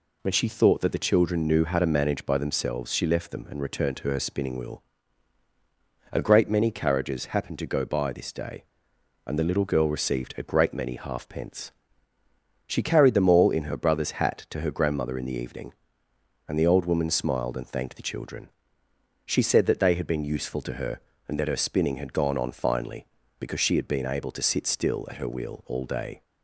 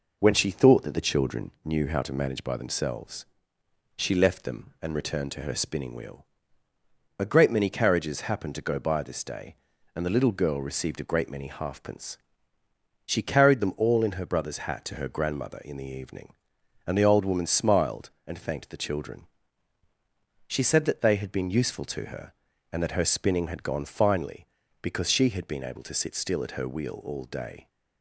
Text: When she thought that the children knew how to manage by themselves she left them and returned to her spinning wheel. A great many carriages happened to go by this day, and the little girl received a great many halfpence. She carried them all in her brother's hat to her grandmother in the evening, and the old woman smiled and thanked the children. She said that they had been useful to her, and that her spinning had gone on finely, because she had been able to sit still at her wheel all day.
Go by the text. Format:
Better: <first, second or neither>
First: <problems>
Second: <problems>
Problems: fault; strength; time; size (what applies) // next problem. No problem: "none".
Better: first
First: none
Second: pauses between "themselves" and "she"; noticeable; at 3.2 s; 0.70 s long // skips "on"; at 23.8 s